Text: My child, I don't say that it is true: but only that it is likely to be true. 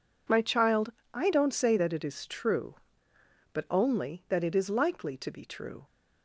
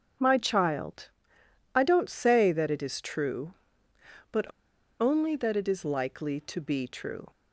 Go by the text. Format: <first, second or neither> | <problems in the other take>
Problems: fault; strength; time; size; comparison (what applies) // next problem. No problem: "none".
first | starts louder than the rest; strong; until 1.8 s; 7.5 dB // pauses between "but" and "only"; noticeable; at 4.5 s; 0.49 s long